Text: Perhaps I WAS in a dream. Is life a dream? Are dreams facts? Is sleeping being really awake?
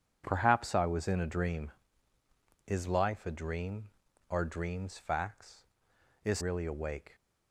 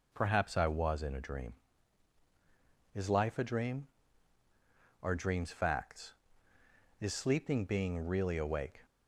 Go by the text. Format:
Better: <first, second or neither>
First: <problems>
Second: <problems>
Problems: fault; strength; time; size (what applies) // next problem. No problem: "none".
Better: second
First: skips "sleeping being"; at 6.3 s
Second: none